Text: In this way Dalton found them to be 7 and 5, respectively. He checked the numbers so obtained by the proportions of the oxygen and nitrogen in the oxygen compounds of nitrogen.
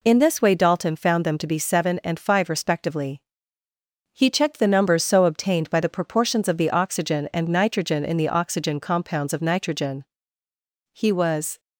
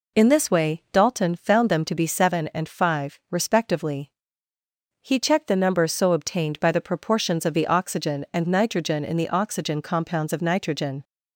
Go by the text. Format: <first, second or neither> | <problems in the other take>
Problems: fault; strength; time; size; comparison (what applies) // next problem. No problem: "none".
second | goes on to say "He was"; noticeable; from 10.9 s on; 0.68 s long